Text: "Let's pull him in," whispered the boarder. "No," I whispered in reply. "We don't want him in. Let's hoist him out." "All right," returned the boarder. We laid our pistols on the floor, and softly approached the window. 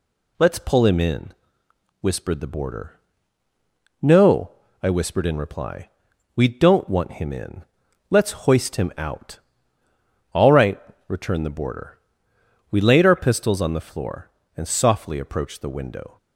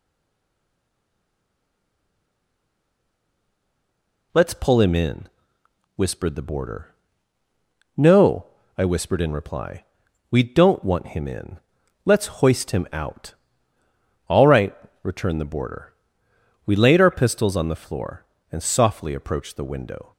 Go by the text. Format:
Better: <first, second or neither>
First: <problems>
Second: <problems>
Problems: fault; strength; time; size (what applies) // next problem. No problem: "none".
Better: first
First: none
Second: stays silent before the first word; strong; until 4.3 s; 4.3 s long